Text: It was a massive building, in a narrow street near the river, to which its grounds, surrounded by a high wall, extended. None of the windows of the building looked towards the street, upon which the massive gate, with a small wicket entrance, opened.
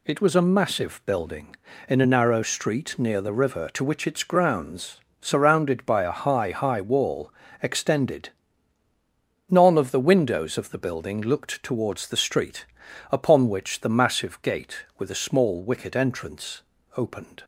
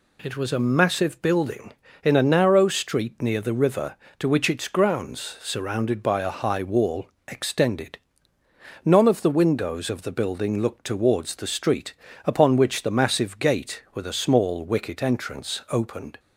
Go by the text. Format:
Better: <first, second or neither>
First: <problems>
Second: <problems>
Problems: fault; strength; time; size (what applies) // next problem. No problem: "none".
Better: second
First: says "high" twice; at 6.5 s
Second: none